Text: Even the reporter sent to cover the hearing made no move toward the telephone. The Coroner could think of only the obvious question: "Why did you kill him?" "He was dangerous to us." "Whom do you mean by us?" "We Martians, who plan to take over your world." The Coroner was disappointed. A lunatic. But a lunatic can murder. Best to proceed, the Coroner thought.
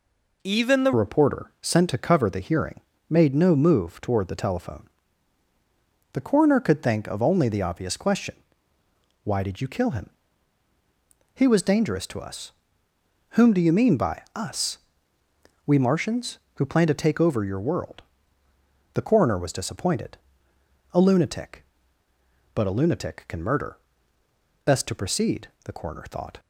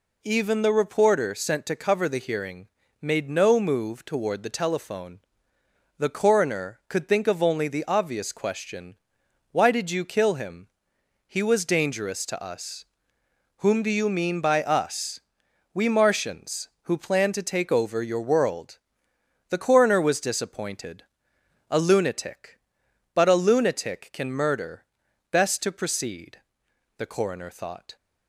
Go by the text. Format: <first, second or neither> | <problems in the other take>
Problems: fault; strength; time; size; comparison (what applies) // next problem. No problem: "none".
second | changes voice at "reporter"; from 0.9 s on; 25.4 s long // pauses between "hearing" and "made"; slight; at 2.8 s; 0.30 s long; slight in the second